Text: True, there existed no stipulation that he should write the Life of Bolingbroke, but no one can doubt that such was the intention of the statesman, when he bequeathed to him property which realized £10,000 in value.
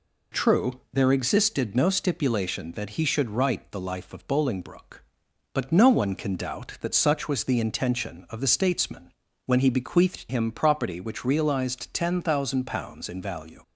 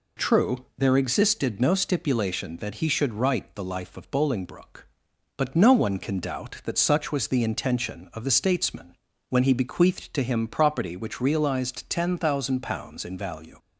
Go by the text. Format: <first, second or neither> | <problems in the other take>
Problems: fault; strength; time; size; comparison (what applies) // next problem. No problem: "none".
second | skips "to"; at 10.2 s